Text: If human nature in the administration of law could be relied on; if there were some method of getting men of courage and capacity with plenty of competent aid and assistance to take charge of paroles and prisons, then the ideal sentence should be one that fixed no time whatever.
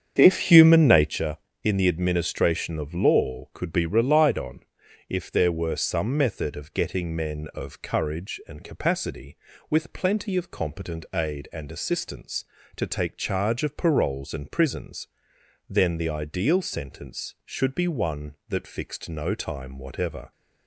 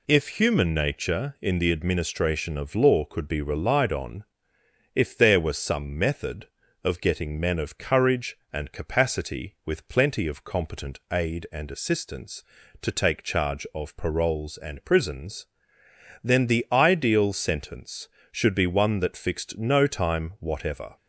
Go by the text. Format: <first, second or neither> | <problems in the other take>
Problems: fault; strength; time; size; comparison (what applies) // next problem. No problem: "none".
second | starts louder than the rest; strong; until 1.2 s; 8 dB